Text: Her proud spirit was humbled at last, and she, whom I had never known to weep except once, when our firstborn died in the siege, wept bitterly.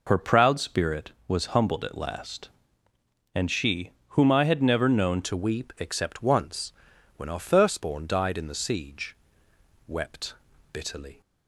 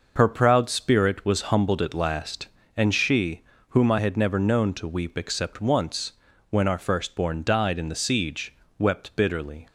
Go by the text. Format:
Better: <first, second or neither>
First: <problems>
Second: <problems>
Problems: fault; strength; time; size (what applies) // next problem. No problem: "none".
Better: second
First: changes voice at "to"; from 5.2 s on; 6.0 s long // pauses between "wept" and "bitterly"; slight; at 10.3 s; 0.36 s long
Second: none